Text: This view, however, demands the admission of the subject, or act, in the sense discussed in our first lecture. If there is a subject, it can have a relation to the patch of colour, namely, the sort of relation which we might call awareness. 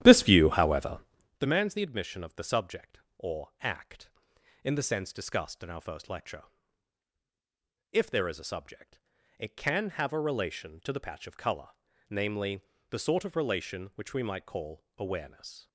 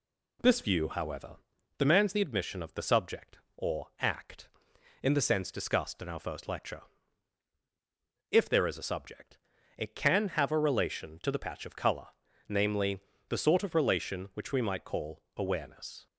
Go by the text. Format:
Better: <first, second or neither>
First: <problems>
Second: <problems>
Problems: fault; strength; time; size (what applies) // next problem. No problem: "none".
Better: second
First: starts louder than the rest; strong; until 1.4 s; 12 dB // pauses between "call" and "awareness"; slight; at 14.8 s; 0.16 s long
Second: pauses between "call" and "awareness"; slight; at 15.2 s; 0.16 s long